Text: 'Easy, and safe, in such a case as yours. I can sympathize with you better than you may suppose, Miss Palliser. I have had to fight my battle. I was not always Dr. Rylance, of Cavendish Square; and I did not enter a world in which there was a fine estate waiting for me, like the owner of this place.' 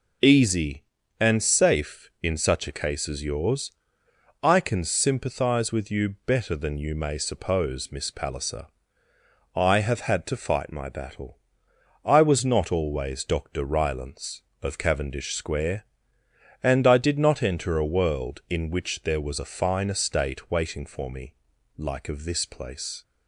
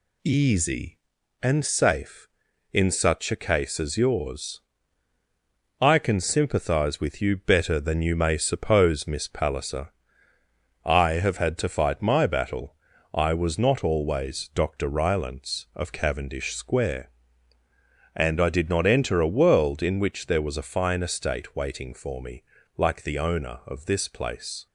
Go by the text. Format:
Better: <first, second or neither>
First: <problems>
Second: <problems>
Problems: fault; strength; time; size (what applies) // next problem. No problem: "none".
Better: second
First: skips "the owner"; at 22.0 s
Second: none